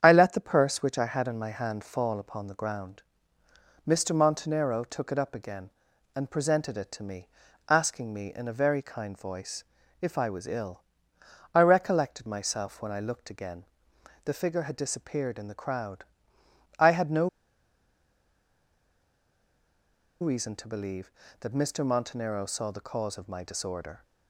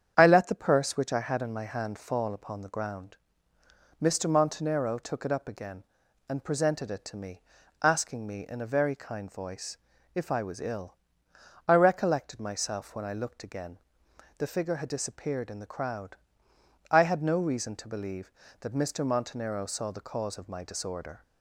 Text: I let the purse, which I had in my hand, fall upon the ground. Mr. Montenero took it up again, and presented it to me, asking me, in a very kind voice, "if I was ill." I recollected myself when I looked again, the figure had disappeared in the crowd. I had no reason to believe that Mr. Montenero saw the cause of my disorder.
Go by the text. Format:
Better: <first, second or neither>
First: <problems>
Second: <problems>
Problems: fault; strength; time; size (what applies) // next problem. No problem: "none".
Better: second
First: starts louder than the rest; strong; until 1.0 s; 8.5 dB // pauses between "no" and "reason"; strong; at 17.2 s; 2.9 s long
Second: starts louder than the rest; strong; until 1.1 s; 8.5 dB